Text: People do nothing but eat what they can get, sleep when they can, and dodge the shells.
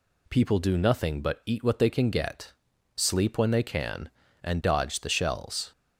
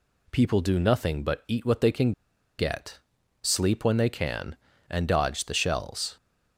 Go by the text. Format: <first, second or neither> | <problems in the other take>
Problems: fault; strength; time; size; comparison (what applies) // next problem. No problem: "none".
first | pauses between "can" and "get"; noticeable; at 2.1 s; 0.46 s long